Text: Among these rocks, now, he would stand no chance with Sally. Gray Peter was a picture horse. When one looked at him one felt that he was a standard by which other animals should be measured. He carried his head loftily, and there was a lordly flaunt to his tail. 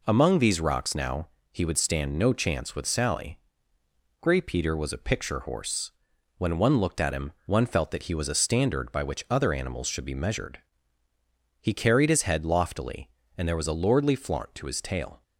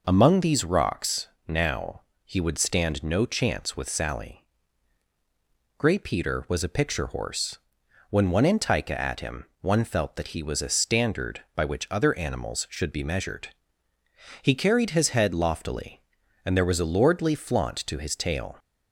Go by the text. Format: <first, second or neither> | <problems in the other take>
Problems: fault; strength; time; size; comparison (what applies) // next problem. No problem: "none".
first | says "antica" for "looked"; at 8.4 s // pauses between "him" and "one"; slight; at 9.4 s; 0.16 s long; slight in the first